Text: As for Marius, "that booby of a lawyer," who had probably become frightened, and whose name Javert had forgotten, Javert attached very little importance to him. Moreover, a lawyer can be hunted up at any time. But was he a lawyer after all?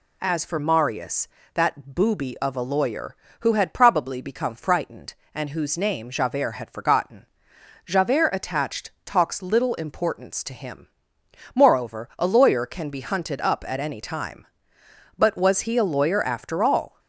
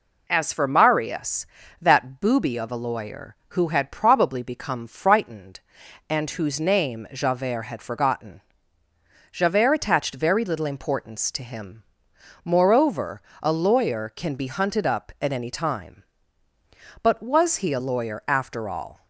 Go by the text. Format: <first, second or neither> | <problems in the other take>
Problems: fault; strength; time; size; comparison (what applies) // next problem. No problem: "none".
second | says "talks" for "very"; at 9.0 s